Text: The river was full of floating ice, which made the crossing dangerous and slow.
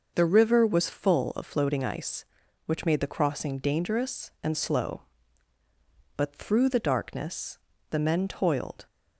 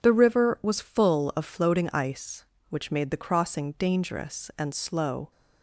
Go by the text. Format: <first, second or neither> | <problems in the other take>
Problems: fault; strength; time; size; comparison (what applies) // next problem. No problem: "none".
second | starts louder than the rest; noticeable; until 1.1 s; 6 dB // goes on to say "But through the darkness the men toiled"; strong; from 6.1 s on; 2.7 s long